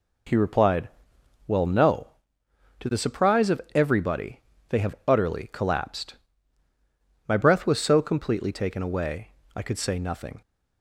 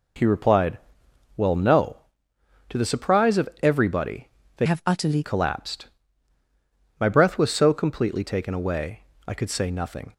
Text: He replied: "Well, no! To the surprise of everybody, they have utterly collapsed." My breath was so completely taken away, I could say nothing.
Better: first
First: none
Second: changes voice from "have" to "utterly"; from 4.6 to 5.2 s; 0.6 s long

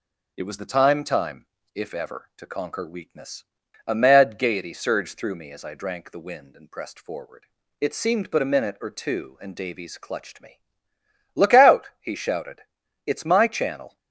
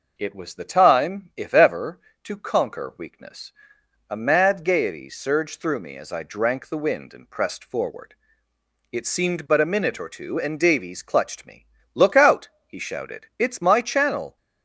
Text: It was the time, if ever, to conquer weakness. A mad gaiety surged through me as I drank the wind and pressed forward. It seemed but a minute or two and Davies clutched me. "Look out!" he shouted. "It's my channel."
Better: second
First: says "time" twice; at 1.0 s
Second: none

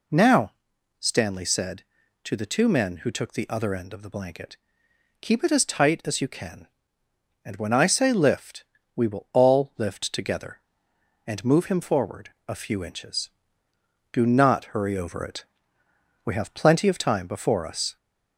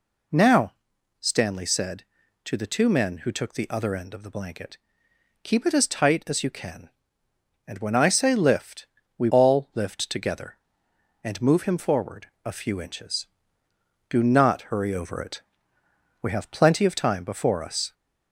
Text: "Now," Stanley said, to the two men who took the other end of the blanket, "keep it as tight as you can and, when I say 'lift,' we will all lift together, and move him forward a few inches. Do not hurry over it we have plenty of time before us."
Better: first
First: pauses between "it" and "we"; noticeable; at 15.4 s; 0.80 s long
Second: skips "will"; at 9.2 s // pauses between "it" and "we"; noticeable; at 15.4 s; 0.80 s long

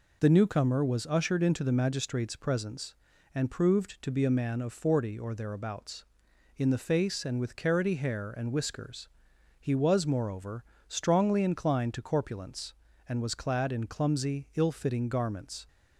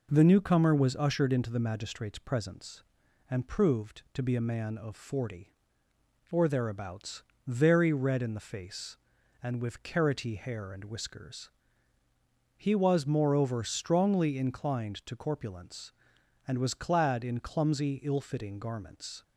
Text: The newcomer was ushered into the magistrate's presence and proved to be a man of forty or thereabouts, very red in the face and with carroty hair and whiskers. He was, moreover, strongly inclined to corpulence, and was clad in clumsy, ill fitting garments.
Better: second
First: skips "very red"; at 6.3 s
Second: none

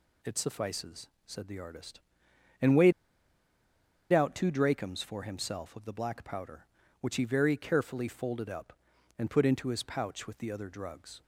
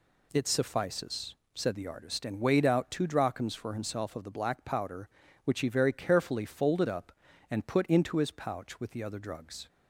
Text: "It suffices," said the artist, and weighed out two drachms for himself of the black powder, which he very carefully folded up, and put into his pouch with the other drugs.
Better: second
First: pauses between "weighed" and "out"; at 2.9 s; 1.1 s long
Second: none

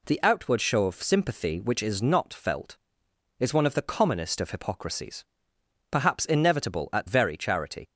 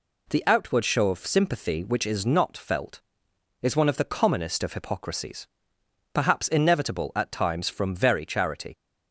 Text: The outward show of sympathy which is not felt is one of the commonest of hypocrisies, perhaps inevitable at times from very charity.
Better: second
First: skips "times from"; at 7.0 s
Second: none

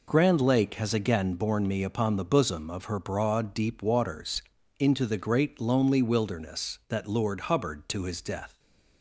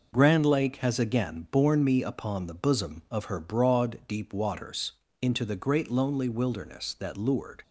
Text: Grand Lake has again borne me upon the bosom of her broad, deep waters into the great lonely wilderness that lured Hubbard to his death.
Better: first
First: pauses between "waters" and "into"; at 4.4 s; 0.38 s long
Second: pauses between "waters" and "into"; slight; at 4.9 s; 0.28 s long // stops before "Hubbard to his death"; at 7.6 s

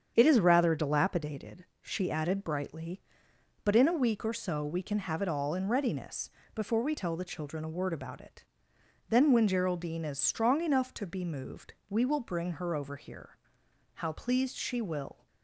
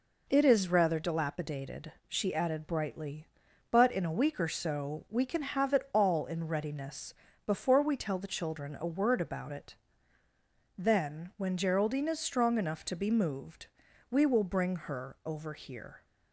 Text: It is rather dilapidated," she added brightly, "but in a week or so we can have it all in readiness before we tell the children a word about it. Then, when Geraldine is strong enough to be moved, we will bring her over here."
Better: second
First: starts louder than the rest; strong; until 1.1 s; 7.5 dB // pauses between "readiness" and "before"; slight; at 6.3 s; 0.24 s long // goes on to say "How pleased she will"; from 13.9 s on; 1.3 s long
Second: pauses between "readiness" and "before"; slight; at 7.1 s; 0.32 s long

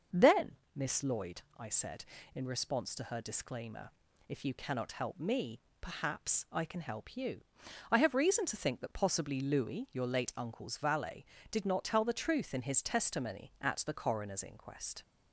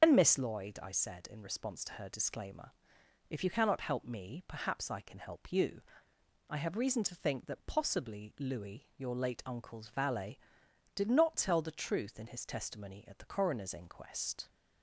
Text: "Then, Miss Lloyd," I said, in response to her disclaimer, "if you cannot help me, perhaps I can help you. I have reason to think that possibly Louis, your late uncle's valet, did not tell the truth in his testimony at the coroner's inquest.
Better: first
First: starts louder than the rest; until 1.3 s; 6.5 dB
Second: loses the start of "Then"; at 0.0 s; 115 ms // starts louder than the rest; noticeable; until 1.0 s; 6 dB

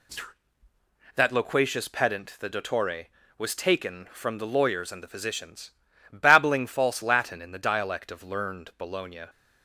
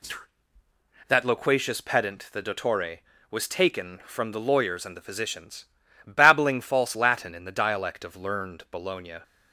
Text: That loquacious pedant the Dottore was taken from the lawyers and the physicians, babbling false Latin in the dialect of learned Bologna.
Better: neither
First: none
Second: none

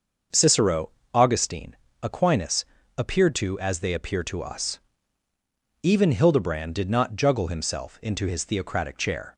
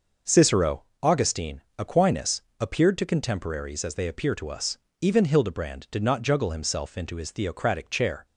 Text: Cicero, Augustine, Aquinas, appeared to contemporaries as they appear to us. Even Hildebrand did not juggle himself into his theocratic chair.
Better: second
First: starts louder than the rest; until 1.5 s; 6.5 dB // skips "contemporaries"; at 3.5 s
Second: none

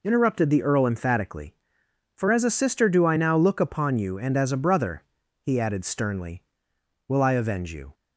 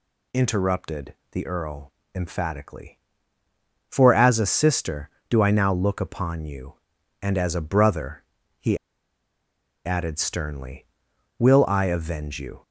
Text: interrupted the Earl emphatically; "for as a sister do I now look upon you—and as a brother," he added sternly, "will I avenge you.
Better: first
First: none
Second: pauses between "interrupted" and "the"; slight; at 1.1 s; 0.18 s long // pauses between "Earl" and "emphatically"; slight; at 1.9 s; 0.22 s long // pauses between "he" and "added"; at 8.7 s; 1.0 s long

